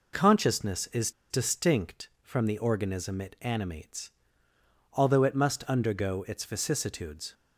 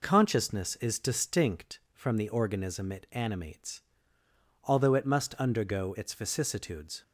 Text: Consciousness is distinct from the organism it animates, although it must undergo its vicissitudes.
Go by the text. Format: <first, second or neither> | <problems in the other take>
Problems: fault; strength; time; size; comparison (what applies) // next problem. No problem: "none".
second | pauses between "is" and "distinct"; slight; at 1.1 s; 0.19 s long